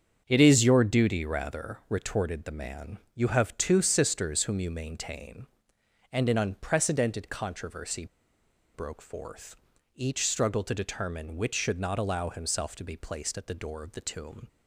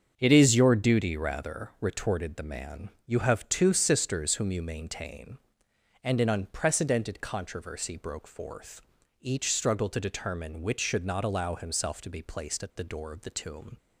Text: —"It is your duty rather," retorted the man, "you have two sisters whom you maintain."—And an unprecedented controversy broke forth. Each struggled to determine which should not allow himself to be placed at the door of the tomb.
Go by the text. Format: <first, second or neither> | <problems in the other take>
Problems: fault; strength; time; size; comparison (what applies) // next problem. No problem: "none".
second | starts louder than the rest; strong; until 1.2 s; 7 dB; strong in the second // pauses between "controversy" and "broke"; noticeable; at 8.0 s; 0.68 s long